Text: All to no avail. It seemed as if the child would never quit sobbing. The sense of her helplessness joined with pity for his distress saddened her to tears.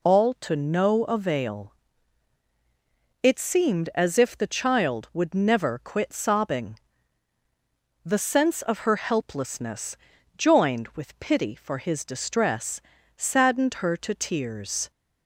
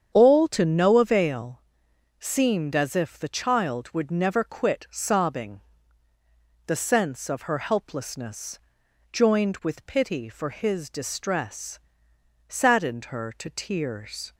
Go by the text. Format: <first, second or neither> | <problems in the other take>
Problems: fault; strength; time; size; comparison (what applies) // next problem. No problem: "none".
first | starts louder than the rest; strong; until 1.1 s; 8 dB // skips "It"; at 1.9 s // pauses between "helplessness" and "joined"; noticeable; at 8.5 s; 0.52 s long; also in the first // pauses between "distress" and "saddened"; noticeable; at 11.8 s; 0.68 s long; also in the first